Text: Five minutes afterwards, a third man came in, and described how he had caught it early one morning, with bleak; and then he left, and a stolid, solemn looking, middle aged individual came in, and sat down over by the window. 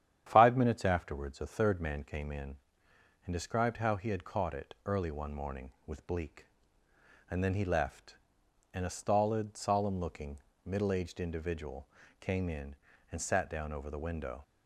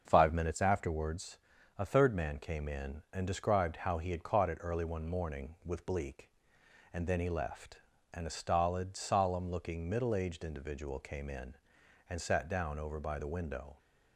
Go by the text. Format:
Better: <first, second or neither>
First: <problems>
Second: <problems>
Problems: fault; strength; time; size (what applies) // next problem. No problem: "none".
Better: second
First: starts louder than the rest; strong; until 1.2 s; 10 dB // pauses between "individual" and "came"; slight; at 11.8 s; 0.32 s long // skips "by"; at 13.8 s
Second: starts louder than the rest; until 1.0 s; 6.5 dB